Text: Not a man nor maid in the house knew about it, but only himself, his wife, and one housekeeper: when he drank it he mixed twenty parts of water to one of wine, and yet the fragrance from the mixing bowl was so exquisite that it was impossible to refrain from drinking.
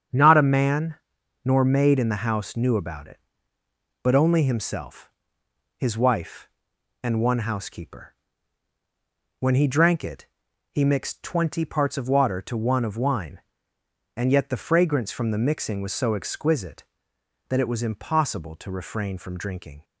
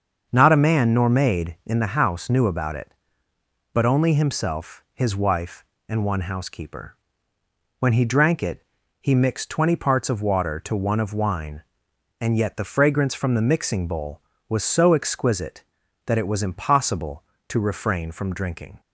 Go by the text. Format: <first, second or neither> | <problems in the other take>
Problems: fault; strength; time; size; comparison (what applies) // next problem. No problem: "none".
second | starts louder than the rest; strong; until 1.6 s; 7.5 dB; also in the second // pauses between "man" and "nor"; noticeable; at 0.9 s; 0.48 s long // pauses between "it" and "he"; noticeable; at 10.2 s; 0.46 s long; also in the second // skips "bowl"; at 15.7 s